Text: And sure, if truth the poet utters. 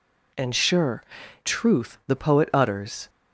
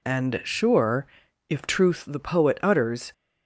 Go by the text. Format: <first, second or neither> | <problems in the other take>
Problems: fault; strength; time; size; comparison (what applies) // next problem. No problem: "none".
second | skips "if"; at 1.2 s